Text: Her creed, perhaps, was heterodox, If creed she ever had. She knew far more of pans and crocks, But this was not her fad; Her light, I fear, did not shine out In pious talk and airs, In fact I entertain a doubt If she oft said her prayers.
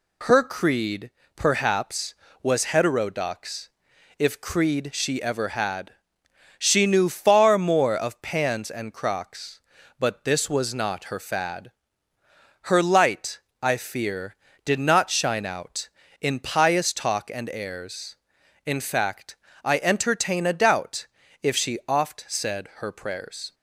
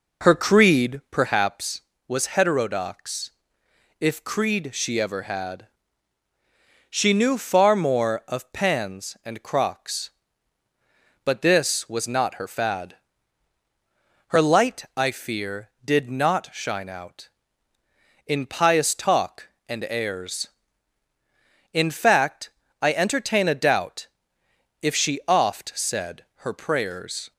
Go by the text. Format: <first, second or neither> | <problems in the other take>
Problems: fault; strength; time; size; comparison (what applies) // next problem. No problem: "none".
first | starts louder than the rest; noticeable; until 1.4 s; 4.5 dB // pauses between "fact" and "I"; slight; at 22.4 s; 0.30 s long; slight in the first // pauses between "doubt" and "If"; noticeable; at 24.0 s; 0.76 s long; slight in the first // pauses between "said" and "her"; slight; at 26.2 s; 0.20 s long